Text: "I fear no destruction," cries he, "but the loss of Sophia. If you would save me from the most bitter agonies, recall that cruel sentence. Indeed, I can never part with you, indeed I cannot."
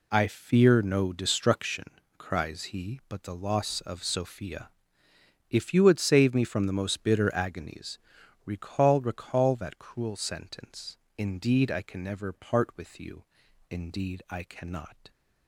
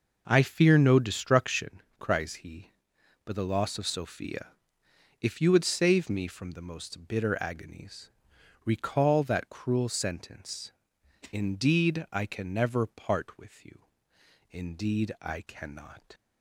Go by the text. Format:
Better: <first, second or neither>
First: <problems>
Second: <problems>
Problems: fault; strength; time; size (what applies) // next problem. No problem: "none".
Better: second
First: says "recall" twice; at 9.0 s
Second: none